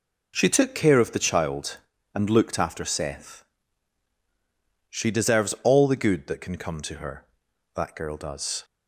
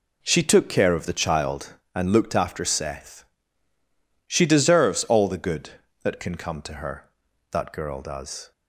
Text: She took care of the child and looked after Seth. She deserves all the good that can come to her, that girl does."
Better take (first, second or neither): neither